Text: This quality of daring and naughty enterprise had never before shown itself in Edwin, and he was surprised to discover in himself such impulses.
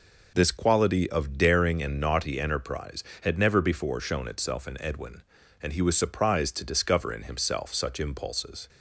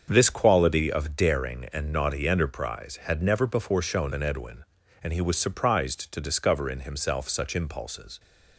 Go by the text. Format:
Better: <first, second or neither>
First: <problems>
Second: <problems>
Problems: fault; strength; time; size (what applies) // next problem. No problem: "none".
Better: first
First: none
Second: starts louder than the rest; until 1.1 s; 7 dB // skips "itself"; at 4.1 s